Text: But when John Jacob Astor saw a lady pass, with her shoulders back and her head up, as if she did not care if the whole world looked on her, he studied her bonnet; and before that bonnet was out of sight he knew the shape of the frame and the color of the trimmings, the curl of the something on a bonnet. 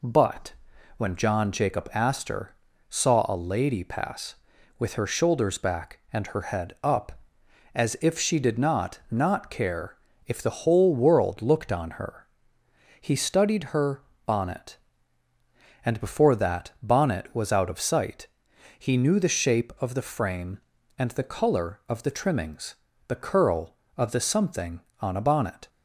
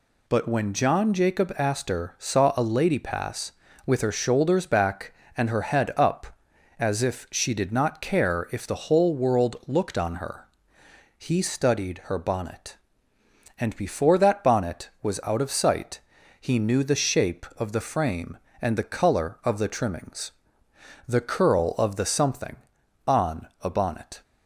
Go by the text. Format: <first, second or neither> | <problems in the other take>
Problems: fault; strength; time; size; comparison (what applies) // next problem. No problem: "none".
second | pauses between "But" and "when"; at 0.5 s; 0.44 s long // pauses between "Astor" and "saw"; slight; at 2.5 s; 0.34 s long // says "not" twice; at 9.1 s // pauses between "care" and "if"; slight; at 9.9 s; 0.30 s long // pauses between "her" and "bonnet"; slight; at 14.0 s; 0.22 s long // pauses between "sight" and "he"; noticeable; at 18.2 s; 0.50 s long; also in the second